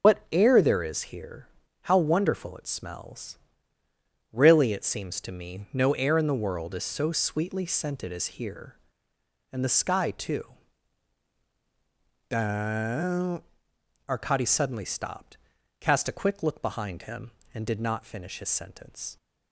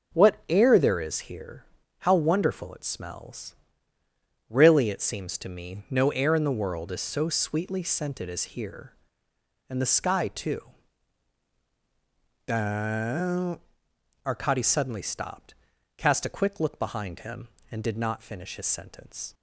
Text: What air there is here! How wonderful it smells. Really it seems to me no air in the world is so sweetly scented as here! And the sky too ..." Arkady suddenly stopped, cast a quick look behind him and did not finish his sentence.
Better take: second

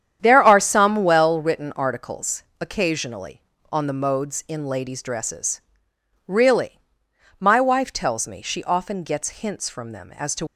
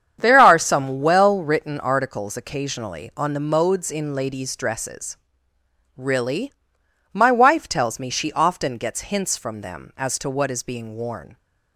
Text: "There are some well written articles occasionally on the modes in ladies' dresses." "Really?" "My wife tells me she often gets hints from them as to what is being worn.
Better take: second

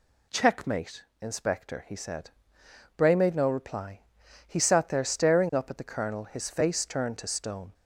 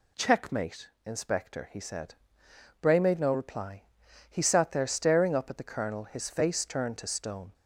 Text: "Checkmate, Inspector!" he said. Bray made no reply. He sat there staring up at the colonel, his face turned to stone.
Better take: neither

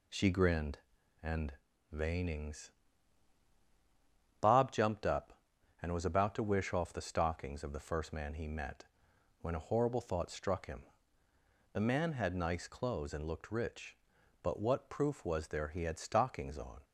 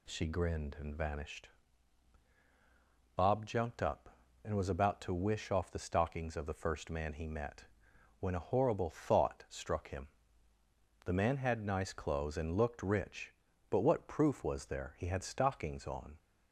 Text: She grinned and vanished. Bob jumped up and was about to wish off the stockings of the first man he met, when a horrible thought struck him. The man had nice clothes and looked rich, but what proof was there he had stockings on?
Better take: second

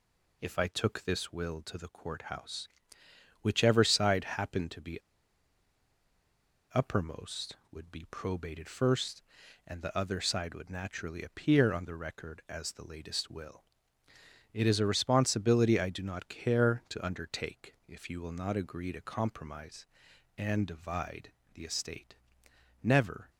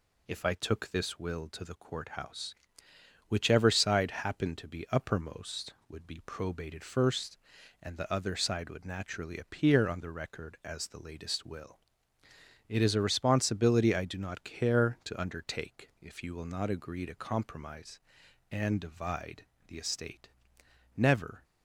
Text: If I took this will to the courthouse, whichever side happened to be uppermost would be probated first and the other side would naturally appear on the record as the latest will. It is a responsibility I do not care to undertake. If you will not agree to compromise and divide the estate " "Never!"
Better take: second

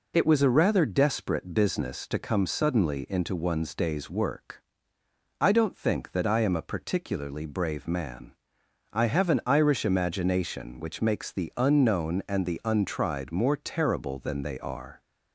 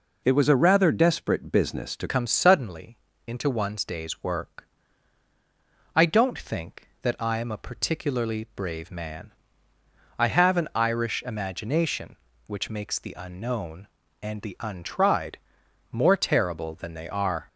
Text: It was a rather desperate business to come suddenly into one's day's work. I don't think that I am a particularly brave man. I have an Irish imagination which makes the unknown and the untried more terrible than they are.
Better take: first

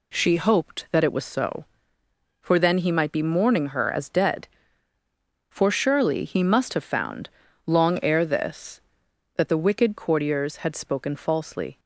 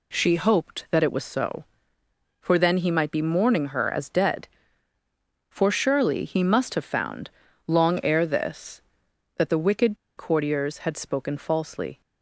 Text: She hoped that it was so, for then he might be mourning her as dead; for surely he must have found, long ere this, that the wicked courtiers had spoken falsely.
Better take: first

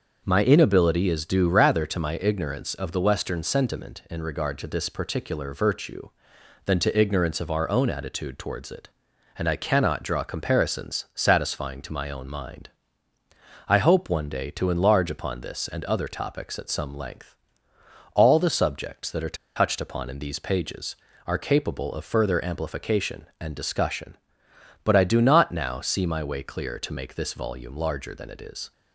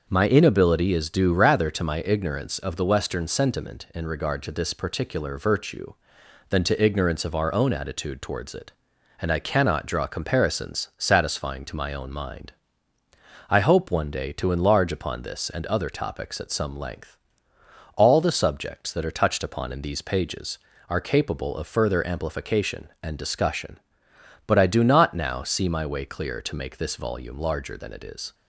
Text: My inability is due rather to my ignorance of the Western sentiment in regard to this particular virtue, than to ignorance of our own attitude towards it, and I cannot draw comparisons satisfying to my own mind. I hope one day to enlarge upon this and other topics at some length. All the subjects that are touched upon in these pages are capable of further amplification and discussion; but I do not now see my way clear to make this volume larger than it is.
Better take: second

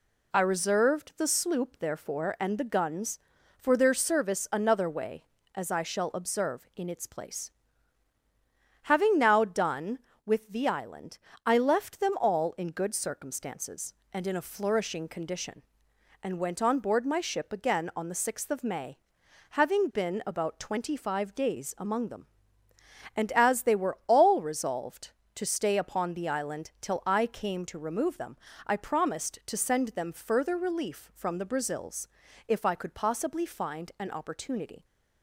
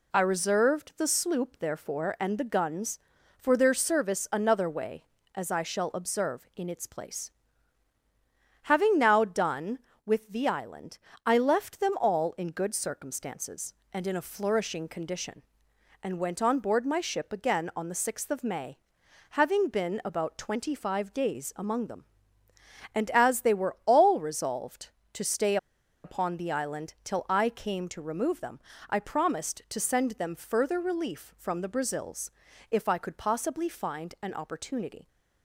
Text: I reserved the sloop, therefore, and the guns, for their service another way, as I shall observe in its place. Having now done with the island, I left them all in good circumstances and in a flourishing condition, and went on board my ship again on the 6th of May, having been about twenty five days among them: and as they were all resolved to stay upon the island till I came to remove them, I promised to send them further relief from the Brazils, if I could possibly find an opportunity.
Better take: first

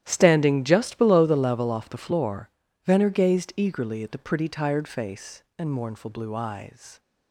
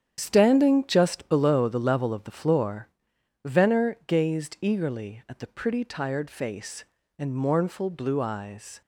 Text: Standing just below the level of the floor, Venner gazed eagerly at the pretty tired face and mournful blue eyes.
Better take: second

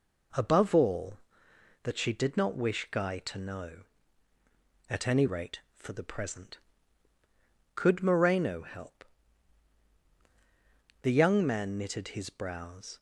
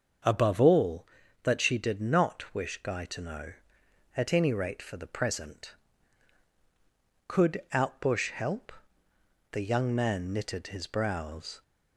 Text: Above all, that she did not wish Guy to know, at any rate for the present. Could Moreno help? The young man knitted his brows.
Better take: first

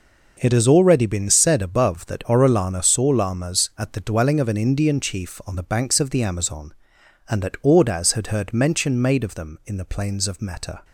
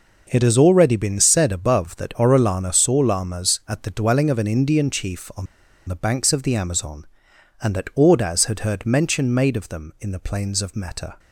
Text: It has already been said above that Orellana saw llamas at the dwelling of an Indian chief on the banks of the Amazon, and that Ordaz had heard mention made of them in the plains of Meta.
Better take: first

